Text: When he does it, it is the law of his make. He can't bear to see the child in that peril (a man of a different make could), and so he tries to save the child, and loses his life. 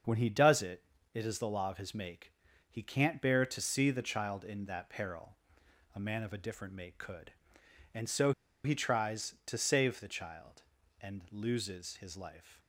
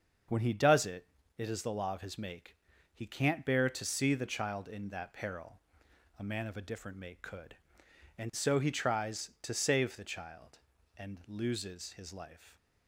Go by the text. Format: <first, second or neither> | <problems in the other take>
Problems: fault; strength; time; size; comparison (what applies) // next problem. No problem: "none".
second | starts louder than the rest; until 1.3 s; 6.5 dB; also in the second // pauses between "so" and "he"; slight; at 8.3 s; 0.33 s long